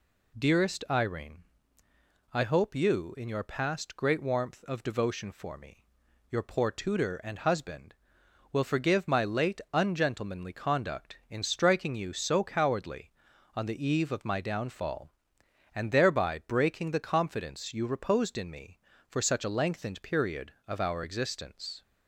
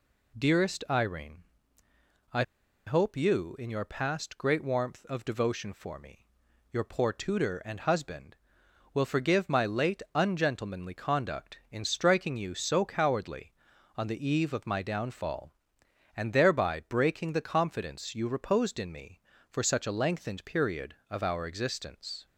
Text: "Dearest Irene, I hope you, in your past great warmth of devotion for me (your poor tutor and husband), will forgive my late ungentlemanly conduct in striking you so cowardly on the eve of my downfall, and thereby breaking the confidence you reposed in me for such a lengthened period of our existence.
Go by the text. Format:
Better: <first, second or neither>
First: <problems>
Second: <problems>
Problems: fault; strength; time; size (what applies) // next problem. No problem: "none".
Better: first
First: none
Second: pauses between "I" and "hope"; at 2.4 s; 0.44 s long